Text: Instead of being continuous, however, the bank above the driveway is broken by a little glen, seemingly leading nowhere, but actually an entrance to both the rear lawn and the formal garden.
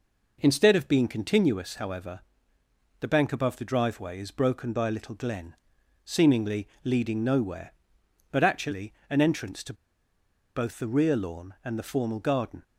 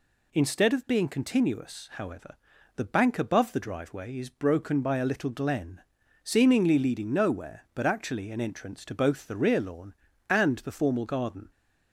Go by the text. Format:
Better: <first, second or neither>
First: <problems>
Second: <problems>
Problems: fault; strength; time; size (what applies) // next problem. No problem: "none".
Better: second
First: pauses between "seemingly" and "leading"; slight; at 6.6 s; 0.18 s long // pauses between "actually" and "an"; slight; at 8.9 s; 0.16 s long // pauses between "to" and "both"; noticeable; at 9.7 s; 0.82 s long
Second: none